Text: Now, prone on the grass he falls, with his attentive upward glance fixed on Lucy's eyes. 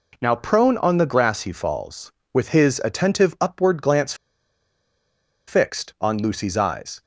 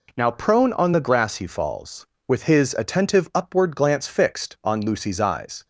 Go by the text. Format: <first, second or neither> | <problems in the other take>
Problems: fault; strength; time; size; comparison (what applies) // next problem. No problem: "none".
second | pauses between "glance" and "fixed"; strong; at 4.1 s; 1.3 s long